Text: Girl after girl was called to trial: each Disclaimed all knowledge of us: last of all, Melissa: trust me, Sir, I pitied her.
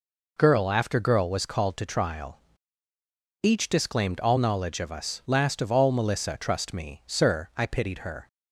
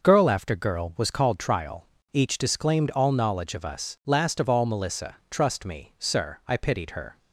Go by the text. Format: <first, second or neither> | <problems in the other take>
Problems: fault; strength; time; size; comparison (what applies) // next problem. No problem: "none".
first | skips "to"; at 1.3 s